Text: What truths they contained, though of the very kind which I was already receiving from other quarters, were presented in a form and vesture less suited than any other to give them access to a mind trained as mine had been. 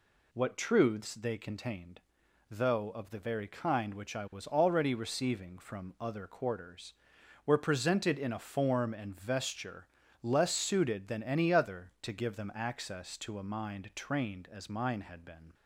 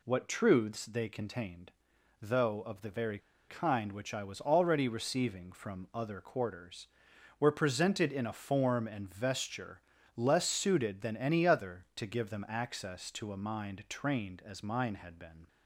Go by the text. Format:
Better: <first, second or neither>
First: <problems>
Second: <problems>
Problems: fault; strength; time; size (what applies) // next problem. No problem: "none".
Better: first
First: pauses between "vesture" and "less"; slight; at 9.8 s; 0.34 s long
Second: pauses between "very" and "kind"; slight; at 3.1 s; 0.29 s long // pauses between "vesture" and "less"; slight; at 9.8 s; 0.34 s long